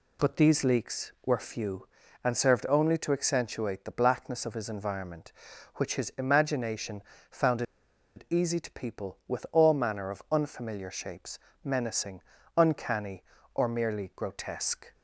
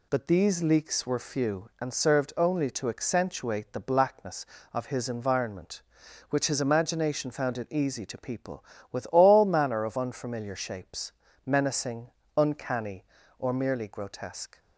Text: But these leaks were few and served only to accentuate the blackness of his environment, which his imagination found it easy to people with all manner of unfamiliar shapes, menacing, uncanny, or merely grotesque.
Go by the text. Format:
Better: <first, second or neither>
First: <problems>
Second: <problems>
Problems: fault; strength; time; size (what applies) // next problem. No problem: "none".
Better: second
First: pauses between "imagination" and "found"; slight; at 7.0 s; 0.28 s long // pauses between "found" and "it"; noticeable; at 7.6 s; 0.53 s long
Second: none